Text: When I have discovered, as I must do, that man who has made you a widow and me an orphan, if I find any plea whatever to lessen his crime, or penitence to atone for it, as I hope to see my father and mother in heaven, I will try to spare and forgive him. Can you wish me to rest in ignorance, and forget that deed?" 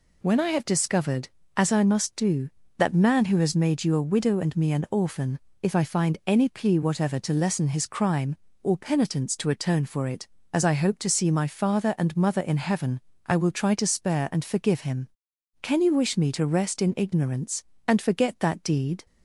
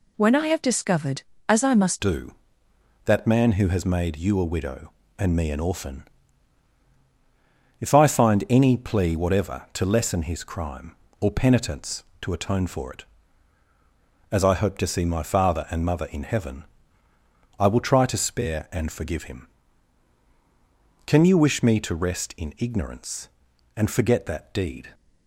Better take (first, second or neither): first